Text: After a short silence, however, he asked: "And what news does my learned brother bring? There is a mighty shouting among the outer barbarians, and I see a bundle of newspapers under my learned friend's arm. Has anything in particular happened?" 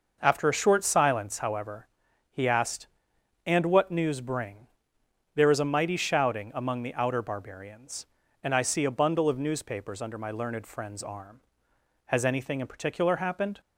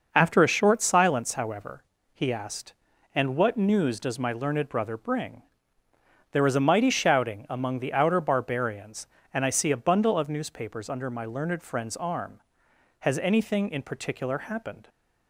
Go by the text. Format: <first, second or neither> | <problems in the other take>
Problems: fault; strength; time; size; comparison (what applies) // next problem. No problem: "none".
second | skips "does my learned brother"; at 4.2 s